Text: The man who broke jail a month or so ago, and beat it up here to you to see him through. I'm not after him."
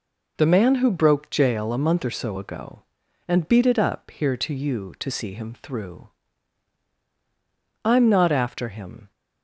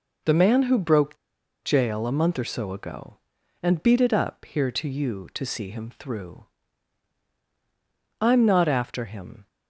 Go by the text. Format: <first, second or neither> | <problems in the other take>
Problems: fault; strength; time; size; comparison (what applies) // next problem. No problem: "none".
first | pauses between "broke" and "jail"; noticeable; at 1.1 s; 0.46 s long